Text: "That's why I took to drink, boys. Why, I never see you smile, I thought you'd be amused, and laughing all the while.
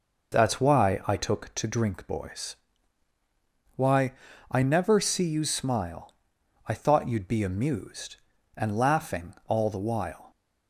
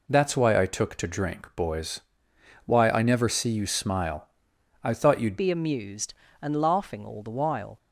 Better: first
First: none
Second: changes voice at "be"; from 5.3 s on; 2.4 s long

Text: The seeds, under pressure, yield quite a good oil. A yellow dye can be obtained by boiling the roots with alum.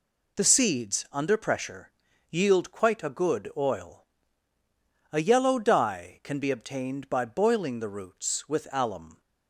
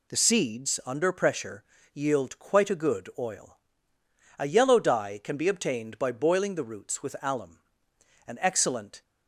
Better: first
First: none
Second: goes on to say "An excellent"; noticeable; from 8.2 s on; 0.74 s long

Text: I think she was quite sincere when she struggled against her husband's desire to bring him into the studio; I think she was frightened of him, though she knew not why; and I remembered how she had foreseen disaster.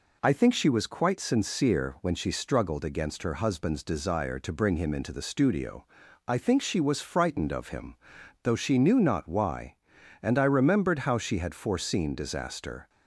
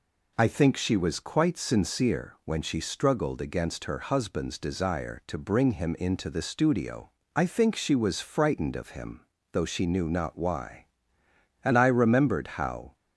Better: first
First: none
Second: stops before "she had foreseen disaster"; at 12.9 s

